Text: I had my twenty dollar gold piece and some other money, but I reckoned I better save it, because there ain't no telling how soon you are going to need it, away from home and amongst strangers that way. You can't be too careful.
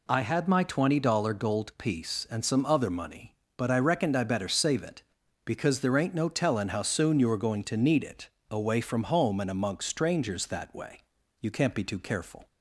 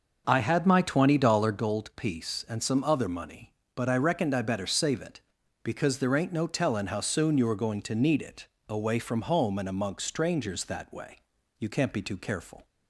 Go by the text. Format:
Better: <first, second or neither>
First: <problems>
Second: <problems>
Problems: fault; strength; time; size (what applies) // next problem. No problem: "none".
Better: first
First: none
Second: starts louder than the rest; until 1.6 s; 6.5 dB